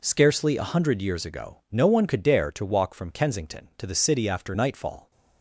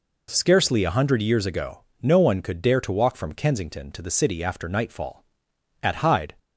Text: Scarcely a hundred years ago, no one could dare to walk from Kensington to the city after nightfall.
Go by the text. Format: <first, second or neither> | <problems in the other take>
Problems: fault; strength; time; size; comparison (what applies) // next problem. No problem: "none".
first | goes on to say "At Hyde"; from 5.8 s on; 0.52 s long